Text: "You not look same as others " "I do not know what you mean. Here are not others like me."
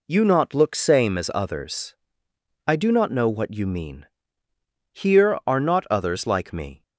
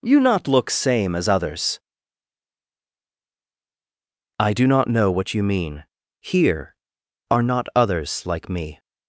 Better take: neither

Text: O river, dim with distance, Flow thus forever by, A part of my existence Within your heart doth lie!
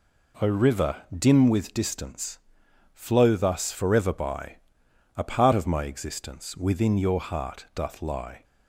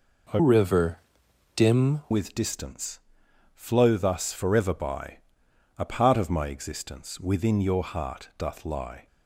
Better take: first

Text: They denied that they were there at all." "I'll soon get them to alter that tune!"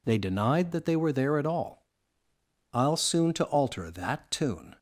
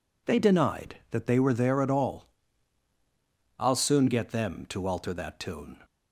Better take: second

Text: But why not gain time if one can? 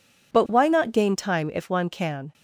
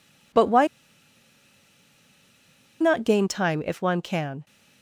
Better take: first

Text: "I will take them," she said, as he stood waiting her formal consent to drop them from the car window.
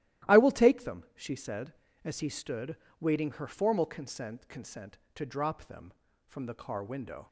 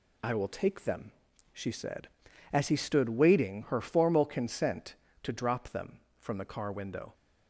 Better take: second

